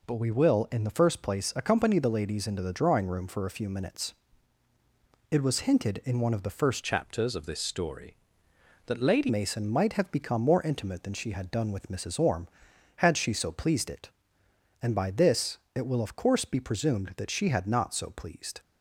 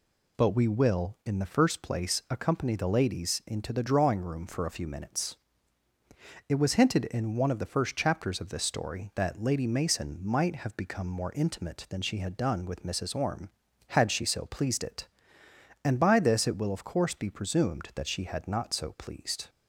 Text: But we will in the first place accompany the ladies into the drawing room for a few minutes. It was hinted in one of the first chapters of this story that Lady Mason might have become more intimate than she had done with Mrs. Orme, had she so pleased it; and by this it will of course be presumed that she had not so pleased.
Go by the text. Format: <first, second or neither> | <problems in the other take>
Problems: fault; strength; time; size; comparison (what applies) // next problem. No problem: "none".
second | changes voice from "chapters" to "Lady"; from 6.8 to 9.2 s; 2.4 s long // pauses between "this" and "it"; slight; at 15.5 s; 0.16 s long